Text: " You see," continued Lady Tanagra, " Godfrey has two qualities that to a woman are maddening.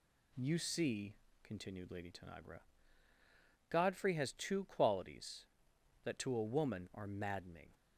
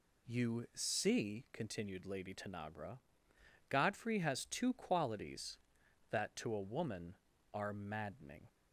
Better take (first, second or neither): neither